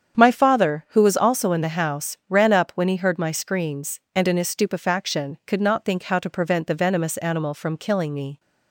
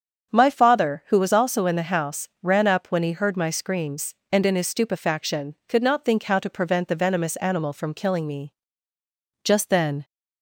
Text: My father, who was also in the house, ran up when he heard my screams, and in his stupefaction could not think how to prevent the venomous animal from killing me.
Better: first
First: starts louder than the rest; strong; until 1.2 s; 8 dB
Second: starts louder than the rest; strong; until 1.3 s; 7.5 dB // goes on to say "Just then"; noticeable; from 9.4 s on; 0.62 s long

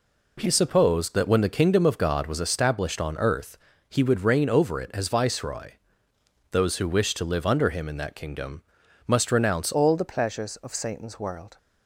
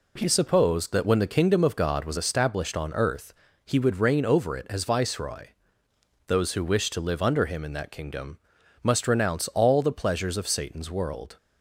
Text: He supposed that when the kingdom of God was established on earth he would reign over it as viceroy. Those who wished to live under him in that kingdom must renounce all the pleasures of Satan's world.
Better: second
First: pauses between "earth" and "he"; slight; at 3.5 s; 0.32 s long // pauses between "kingdom" and "must"; at 8.6 s; 0.44 s long // changes voice at "all"; from 9.7 s on; 1.8 s long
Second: pauses between "earth" and "he"; slight; at 3.3 s; 0.32 s long // pauses between "kingdom" and "must"; at 8.3 s; 0.44 s long

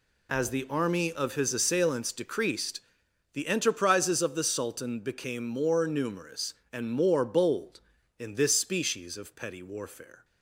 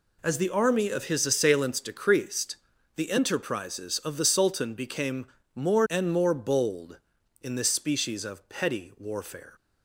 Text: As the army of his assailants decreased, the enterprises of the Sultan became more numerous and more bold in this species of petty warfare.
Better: first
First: none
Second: pauses between "became" and "more"; slight; at 5.2 s; 0.30 s long // skips "numerous"; at 5.8 s

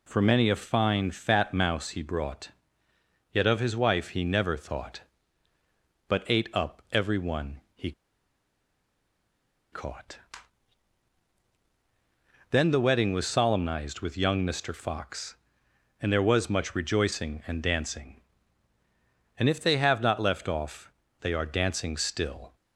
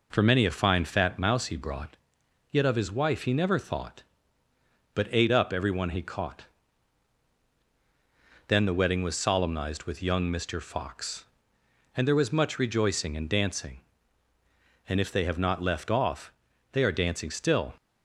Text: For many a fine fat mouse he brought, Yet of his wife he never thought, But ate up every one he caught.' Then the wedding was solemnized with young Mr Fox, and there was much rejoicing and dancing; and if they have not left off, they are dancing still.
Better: second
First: pauses between "one" and "he"; slight; at 7.5 s; 0.16 s long // pauses between "he" and "caught"; strong; at 7.9 s; 1.8 s long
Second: none

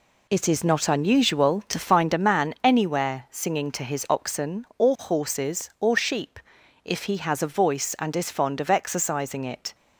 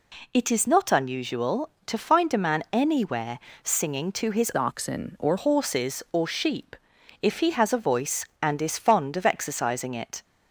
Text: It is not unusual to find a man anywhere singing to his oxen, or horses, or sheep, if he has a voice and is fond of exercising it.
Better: first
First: none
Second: pauses between "anywhere" and "singing"; slight; at 3.3 s; 0.24 s long // changes voice from "oxen" to "or"; from 4.5 to 5.3 s; 0.8 s long

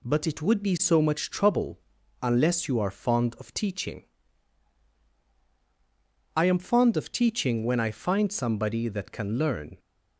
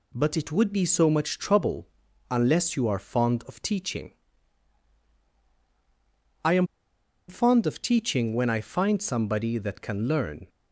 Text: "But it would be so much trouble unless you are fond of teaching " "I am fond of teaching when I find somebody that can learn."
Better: first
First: pauses between "trouble" and "unless"; at 1.7 s; 0.42 s long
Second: pauses between "trouble" and "unless"; at 1.8 s; 0.42 s long // pauses between "am" and "fond"; noticeable; at 6.6 s; 0.61 s long

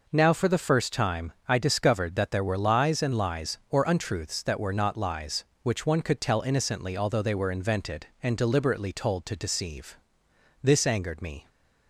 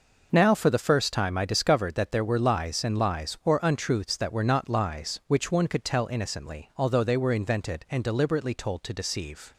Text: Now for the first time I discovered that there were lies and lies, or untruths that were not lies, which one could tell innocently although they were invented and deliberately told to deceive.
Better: second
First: goes on to say "This angered me"; noticeable; from 10.6 s on; 0.86 s long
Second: none

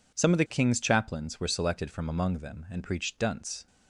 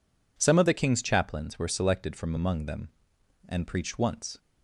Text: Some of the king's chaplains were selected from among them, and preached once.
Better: second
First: says "dunce" for "once"; at 3.1 s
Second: none

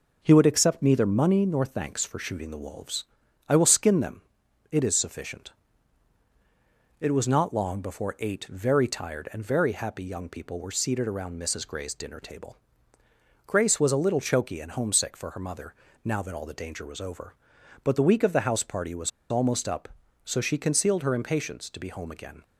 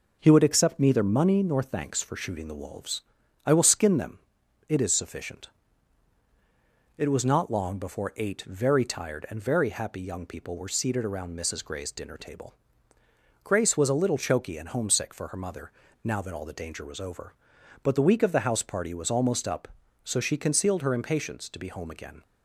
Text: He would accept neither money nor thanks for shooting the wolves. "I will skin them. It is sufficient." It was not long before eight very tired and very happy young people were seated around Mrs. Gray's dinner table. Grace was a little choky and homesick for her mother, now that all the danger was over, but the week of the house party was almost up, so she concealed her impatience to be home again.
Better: second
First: pauses between "was" and "almost"; slight; at 19.1 s; 0.20 s long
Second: none

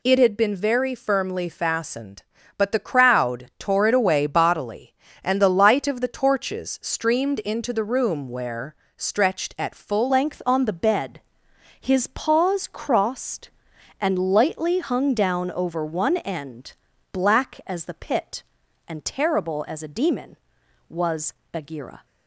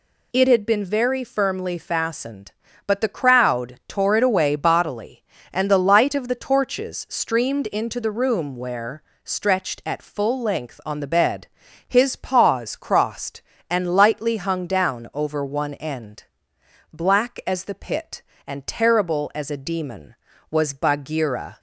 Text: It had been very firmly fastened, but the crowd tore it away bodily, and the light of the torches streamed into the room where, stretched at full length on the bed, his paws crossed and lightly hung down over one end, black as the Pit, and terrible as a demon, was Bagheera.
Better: second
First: changes voice at "length"; from 10.0 s on; 12.0 s long // pauses between "was" and "Bagheera"; slight; at 21.3 s; 0.20 s long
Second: none

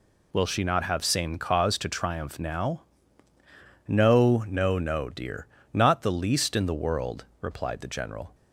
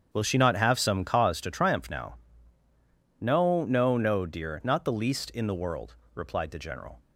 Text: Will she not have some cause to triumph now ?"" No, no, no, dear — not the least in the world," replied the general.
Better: second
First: says "same" for "some"; at 1.0 s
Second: none

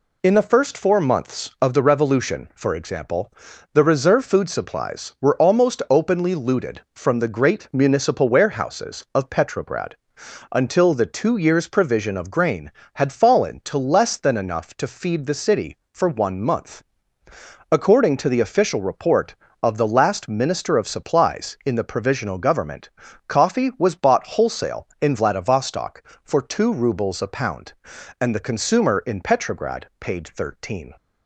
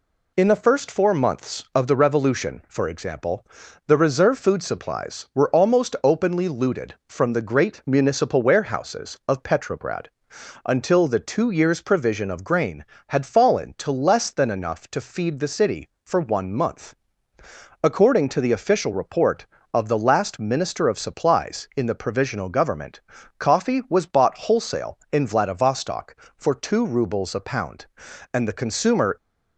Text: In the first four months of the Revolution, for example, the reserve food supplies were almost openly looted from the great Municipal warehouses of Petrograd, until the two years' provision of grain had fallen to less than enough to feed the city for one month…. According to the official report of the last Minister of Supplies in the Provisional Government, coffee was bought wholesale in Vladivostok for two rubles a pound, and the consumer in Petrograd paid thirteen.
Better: first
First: none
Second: stops before "in Petrograd paid thirteen"; at 29.1 s

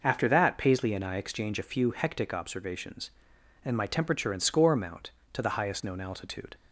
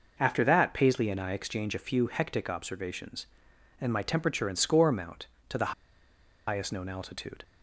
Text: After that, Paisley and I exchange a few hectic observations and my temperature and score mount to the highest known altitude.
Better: first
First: none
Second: pauses between "the" and "highest"; noticeable; at 5.7 s; 0.74 s long

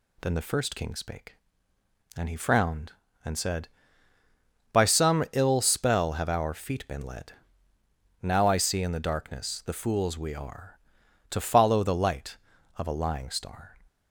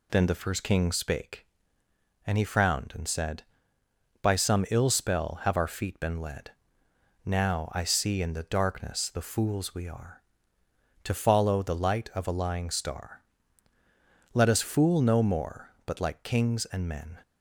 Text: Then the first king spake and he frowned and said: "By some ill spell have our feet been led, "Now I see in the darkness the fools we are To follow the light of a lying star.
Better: first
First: none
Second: goes on to say "Let us fool no more but like kings and men"; strong; from 14.3 s on; 2.8 s long

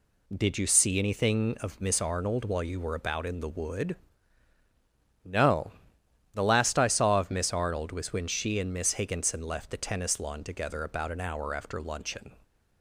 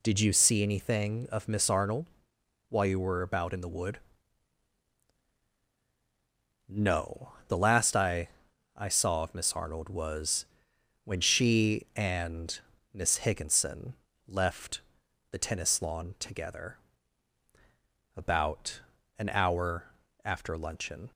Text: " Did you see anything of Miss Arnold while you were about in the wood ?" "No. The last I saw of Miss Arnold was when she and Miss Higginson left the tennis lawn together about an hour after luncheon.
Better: first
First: none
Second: pauses between "Arnold" and "while"; noticeable; at 2.0 s; 0.60 s long // says "I" twice; at 8.7 s // pauses between "was" and "when"; noticeable; at 10.4 s; 0.58 s long // pauses between "and" and "Miss"; slight; at 12.5 s; 0.32 s long // pauses between "Higginson" and "left"; slight; at 13.9 s; 0.32 s long // pauses between "left" and "the"; noticeable; at 14.8 s; 0.48 s long // pauses between "together" and "about"; strong; at 16.7 s; 1.3 s long // pauses between "about" and "an"; at 18.8 s; 0.38 s long // pauses between "hour" and "after"; at 19.8 s; 0.38 s long

